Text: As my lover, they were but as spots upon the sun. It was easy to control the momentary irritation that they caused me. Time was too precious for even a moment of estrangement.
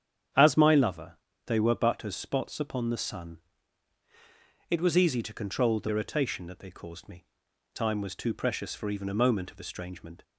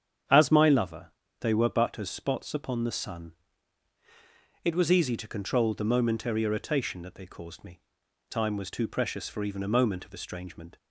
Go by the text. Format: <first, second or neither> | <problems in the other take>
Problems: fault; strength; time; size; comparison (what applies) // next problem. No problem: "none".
second | starts louder than the rest; strong; until 1.6 s; 8.5 dB; strong in the second // skips "momentary"; at 5.8 s